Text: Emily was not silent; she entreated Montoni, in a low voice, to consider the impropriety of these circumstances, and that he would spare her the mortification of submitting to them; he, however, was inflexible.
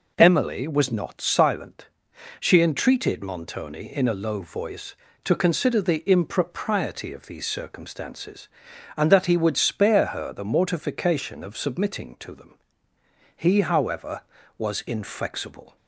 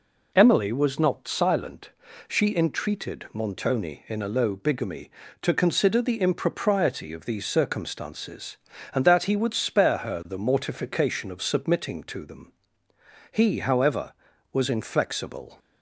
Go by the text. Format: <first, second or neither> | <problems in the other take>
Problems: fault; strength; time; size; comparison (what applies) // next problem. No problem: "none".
first | says "bigamy" for "voice"; at 4.5 s